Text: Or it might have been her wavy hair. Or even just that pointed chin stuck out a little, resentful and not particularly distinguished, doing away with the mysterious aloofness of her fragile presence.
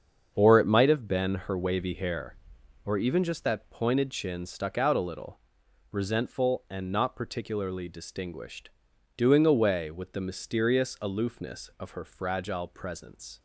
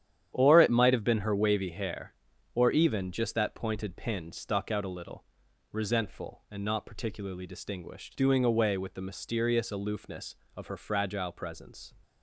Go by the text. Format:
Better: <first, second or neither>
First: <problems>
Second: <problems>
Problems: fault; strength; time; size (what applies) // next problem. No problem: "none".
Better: first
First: starts louder than the rest; until 1.3 s; 7 dB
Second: starts louder than the rest; strong; until 1.3 s; 10 dB // says "pin" for "chin"; at 3.9 s